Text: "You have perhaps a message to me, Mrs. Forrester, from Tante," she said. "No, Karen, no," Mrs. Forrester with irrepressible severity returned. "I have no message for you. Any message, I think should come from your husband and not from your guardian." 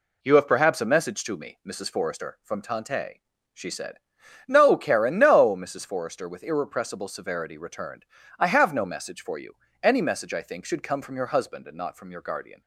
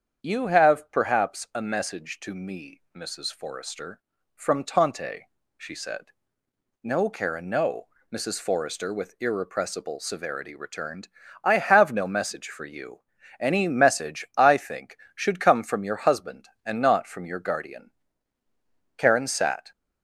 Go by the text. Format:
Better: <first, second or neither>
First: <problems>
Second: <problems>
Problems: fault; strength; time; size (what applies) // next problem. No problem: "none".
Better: first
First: none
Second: starts louder than the rest; strong; until 1.2 s; 8 dB // goes on to say "Karen sat"; noticeable; from 18.9 s on; 0.74 s long